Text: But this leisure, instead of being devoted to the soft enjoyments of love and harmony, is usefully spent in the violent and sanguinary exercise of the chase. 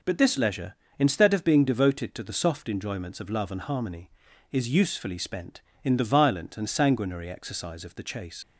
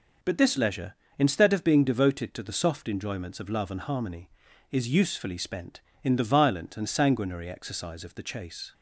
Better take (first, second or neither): second